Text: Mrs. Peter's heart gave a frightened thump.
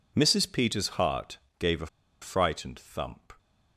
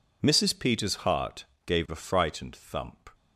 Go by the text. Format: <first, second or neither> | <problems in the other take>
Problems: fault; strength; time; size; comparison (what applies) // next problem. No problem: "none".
second | pauses between "heart" and "gave"; slight; at 1.3 s; 0.20 s long; slight in the second // pauses between "a" and "frightened"; slight; at 1.8 s; 0.35 s long